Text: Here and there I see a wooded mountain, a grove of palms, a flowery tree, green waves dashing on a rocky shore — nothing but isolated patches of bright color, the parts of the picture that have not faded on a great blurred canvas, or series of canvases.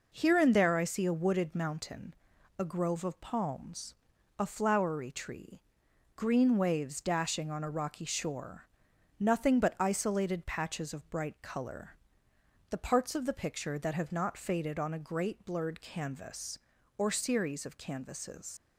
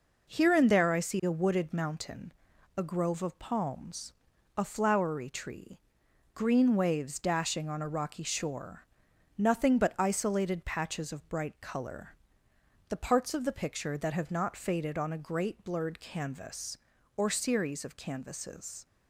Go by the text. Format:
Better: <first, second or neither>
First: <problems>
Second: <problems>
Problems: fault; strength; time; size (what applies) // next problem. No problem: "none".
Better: second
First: leaves "canvases" unfinished; at 18.5 s; 90 ms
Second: none